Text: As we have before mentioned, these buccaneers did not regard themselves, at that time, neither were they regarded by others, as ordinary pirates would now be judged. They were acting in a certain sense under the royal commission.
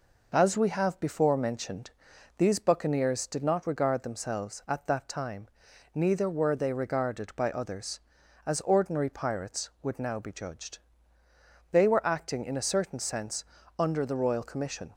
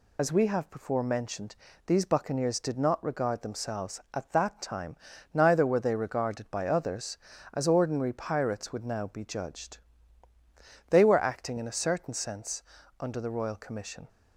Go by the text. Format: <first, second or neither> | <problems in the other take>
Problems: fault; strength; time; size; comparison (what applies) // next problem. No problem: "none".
first | loses the start of "As"; at 0.1 s; 70 ms // pauses between "sense" and "under"; at 12.6 s; 0.38 s long; slight in the first